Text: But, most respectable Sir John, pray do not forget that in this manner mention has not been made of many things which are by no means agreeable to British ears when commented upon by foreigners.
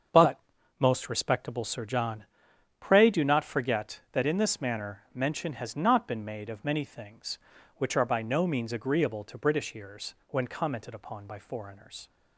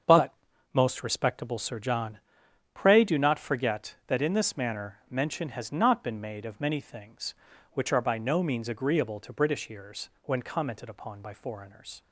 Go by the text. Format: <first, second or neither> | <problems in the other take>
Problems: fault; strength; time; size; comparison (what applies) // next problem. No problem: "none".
neither | starts louder than the rest; the same in both